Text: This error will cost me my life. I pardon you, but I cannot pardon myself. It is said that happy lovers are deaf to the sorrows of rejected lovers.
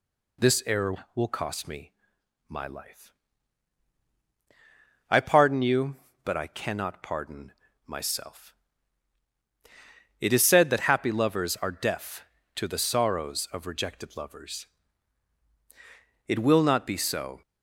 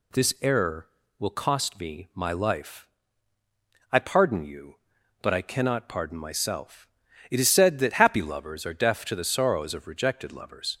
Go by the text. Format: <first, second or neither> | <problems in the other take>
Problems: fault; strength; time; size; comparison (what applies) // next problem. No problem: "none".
second | pauses between "me" and "my"; noticeable; at 1.9 s; 0.56 s long // pauses between "pardon" and "myself"; slight; at 7.5 s; 0.34 s long // goes on to say "It will not be so"; noticeable; from 16.2 s on; 1.1 s long